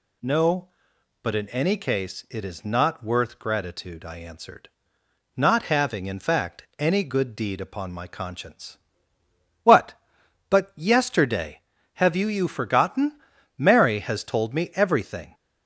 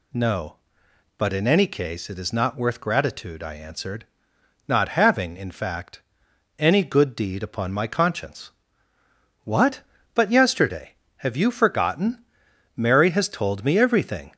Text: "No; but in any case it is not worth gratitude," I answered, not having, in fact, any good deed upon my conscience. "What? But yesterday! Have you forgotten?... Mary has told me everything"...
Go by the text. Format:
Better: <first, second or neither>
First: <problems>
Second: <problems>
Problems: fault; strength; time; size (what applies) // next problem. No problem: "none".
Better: second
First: says "you" twice; at 12.2 s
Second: none